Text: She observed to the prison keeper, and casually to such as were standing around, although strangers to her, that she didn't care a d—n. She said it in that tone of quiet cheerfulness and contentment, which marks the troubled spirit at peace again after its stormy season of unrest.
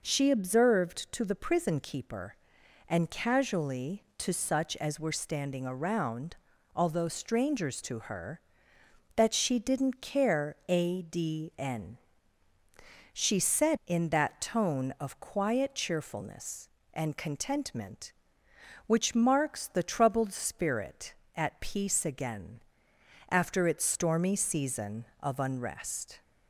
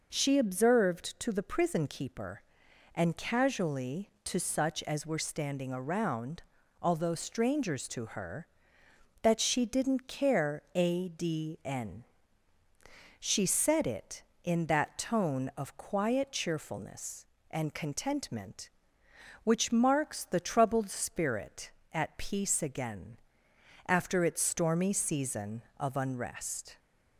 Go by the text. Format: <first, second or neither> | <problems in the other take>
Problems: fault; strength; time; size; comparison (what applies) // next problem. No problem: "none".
second | skips "it"; at 13.8 s // pauses between "again" and "after"; noticeable; at 22.5 s; 0.70 s long; noticeable in the second